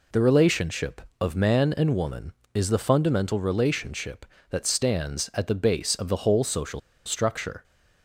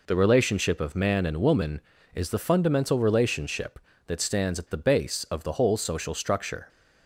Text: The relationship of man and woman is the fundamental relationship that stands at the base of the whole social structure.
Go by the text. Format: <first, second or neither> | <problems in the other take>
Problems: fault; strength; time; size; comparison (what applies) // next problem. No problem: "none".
second | pauses between "social" and "structure"; slight; at 6.8 s; 0.27 s long